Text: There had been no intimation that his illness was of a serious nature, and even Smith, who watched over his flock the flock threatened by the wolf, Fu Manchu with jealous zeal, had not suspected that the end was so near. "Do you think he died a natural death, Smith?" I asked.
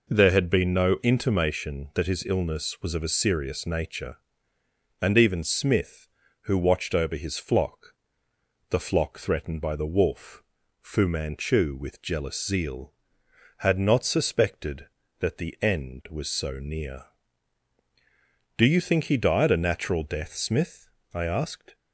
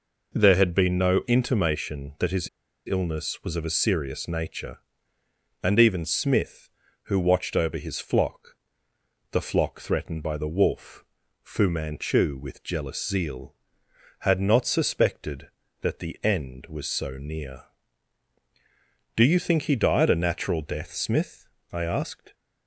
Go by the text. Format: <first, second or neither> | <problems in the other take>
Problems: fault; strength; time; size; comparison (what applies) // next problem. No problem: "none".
first | pauses between "his" and "illness"; at 2.4 s; 0.37 s long // pauses between "flock" and "the"; noticeable; at 8.5 s; 0.76 s long; noticeable in the first